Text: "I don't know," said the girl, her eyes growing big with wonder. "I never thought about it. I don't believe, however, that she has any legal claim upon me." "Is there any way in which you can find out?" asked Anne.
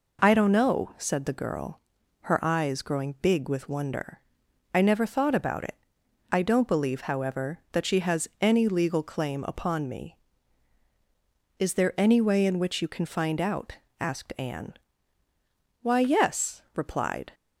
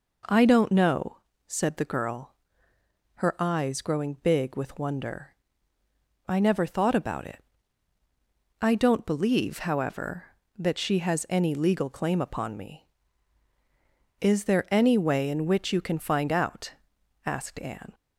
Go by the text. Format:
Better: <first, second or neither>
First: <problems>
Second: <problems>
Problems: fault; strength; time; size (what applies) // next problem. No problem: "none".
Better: second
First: goes on to say "Why yes replied"; from 15.8 s on; 1.5 s long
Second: none